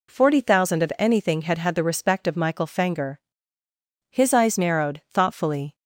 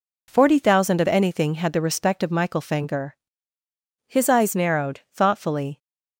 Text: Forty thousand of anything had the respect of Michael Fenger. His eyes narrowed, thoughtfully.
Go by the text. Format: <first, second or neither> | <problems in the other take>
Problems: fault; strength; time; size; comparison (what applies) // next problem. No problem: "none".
second | says "had" twice; at 1.5 s